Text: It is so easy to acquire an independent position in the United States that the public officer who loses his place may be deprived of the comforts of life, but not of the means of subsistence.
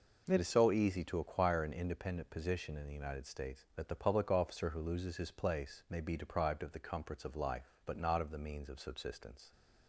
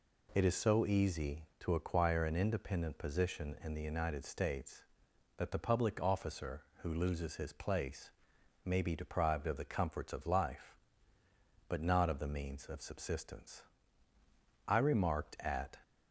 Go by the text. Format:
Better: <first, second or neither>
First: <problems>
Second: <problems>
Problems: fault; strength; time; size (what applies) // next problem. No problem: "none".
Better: first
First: none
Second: pauses between "place" and "may"; noticeable; at 8.0 s; 0.54 s long // goes on to say "I remarked at"; noticeable; from 14.6 s on; 1.0 s long